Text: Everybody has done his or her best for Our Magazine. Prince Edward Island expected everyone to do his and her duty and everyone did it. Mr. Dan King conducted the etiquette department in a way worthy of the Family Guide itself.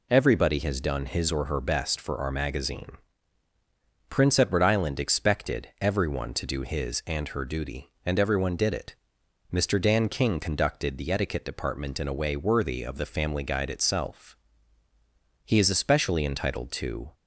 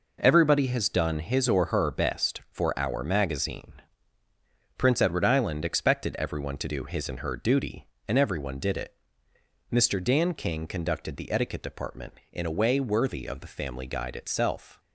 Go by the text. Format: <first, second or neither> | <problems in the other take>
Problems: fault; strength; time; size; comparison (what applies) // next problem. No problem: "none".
second | goes on to say "He is especially entitled to"; strong; from 15.4 s on; 1.6 s long